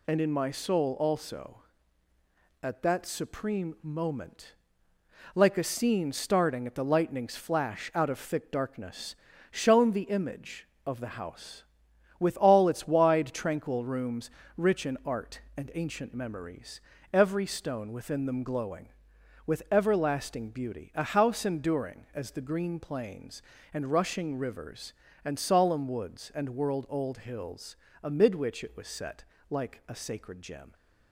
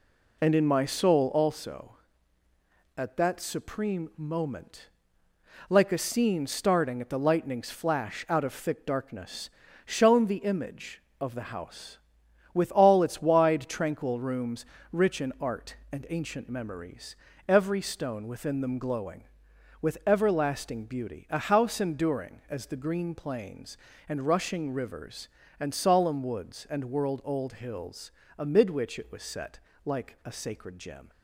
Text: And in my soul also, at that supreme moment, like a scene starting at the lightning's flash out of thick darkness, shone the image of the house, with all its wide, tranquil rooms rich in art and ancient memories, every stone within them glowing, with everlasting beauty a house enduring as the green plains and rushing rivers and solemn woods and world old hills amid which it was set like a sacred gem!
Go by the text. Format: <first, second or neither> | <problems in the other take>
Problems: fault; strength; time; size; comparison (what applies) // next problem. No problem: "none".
first | starts louder than the rest; slight; until 1.6 s; 3 dB // pauses between "rooms" and "rich"; slight; at 14.6 s; 0.28 s long; slight in the first // pauses between "hills" and "amid"; slight; at 28.1 s; 0.28 s long; slight in the first // pauses between "set" and "like"; slight; at 29.5 s; 0.26 s long; slight in the first